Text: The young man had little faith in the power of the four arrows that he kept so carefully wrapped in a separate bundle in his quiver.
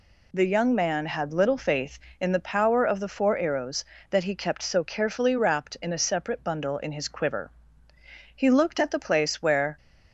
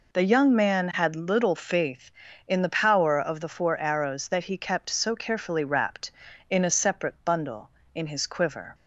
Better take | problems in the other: second | goes on to say "He looked at the place where"; from 8.3 s on; 1.4 s long

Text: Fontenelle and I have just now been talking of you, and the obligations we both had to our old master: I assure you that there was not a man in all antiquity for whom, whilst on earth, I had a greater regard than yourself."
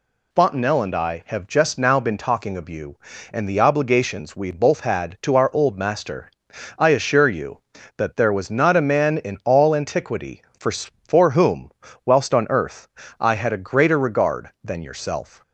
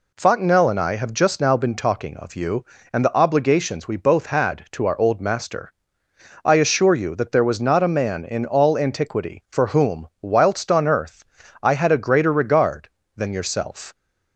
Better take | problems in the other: second | says "for" twice; at 10.7 s

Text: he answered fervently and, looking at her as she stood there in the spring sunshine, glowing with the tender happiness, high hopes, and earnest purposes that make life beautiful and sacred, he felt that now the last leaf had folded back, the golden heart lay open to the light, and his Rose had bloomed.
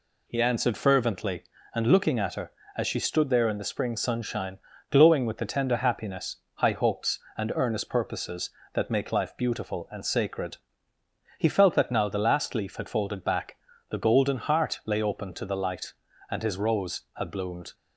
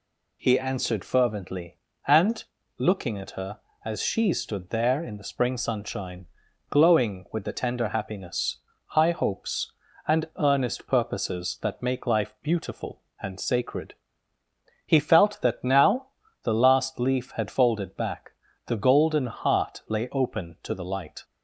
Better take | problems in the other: first | pauses between "now" and "the"; slight; at 16.0 s; 0.36 s long // stops before "and his Rose had bloomed"; at 21.2 s

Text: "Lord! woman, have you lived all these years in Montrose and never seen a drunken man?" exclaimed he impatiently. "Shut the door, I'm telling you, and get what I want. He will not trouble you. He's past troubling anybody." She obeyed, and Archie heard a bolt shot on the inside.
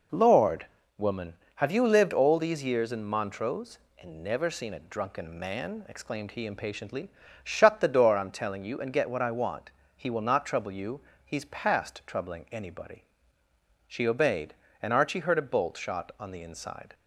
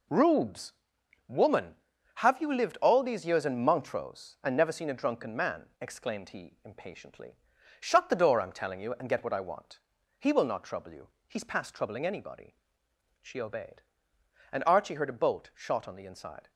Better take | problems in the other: first | says "Rubes" for "Lord"; at 0.0 s

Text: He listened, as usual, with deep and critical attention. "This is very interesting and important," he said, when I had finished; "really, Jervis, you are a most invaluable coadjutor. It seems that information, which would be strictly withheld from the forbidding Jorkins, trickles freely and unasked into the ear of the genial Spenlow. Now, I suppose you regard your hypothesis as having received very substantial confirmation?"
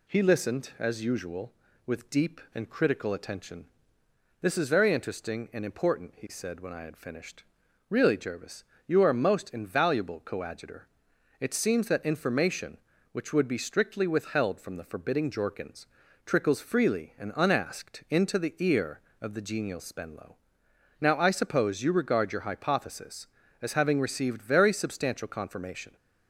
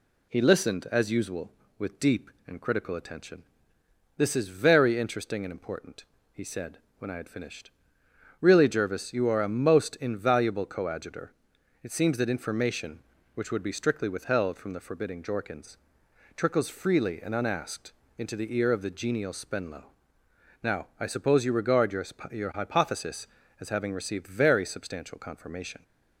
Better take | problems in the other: first | pauses between "unasked" and "into"; slight; at 17.9 s; 0.24 s long // says "your" twice; at 22.2 s

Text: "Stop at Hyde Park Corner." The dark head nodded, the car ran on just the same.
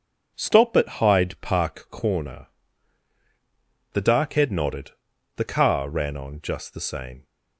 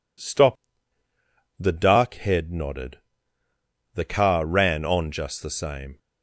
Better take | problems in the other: first | skips "at Hyde Park Corner"; at 1.0 s

